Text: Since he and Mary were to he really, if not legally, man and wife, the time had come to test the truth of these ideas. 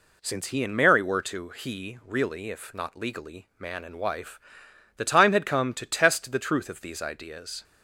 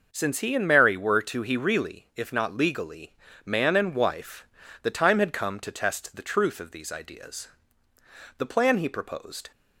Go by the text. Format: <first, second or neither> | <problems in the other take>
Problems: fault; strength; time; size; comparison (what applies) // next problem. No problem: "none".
first | goes on to say "The plan he proposed"; noticeable; from 8.3 s on; 1.1 s long